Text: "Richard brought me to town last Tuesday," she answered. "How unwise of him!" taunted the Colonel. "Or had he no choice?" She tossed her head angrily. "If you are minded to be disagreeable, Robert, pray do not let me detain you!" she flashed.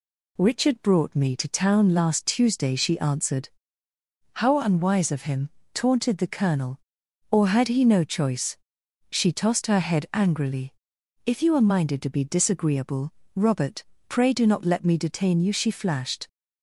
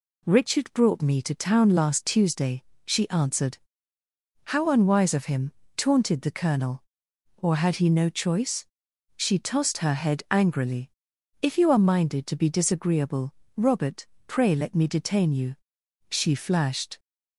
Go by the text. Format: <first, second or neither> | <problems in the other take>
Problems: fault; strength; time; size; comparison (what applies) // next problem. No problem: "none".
first | skips "do not"; at 14.5 s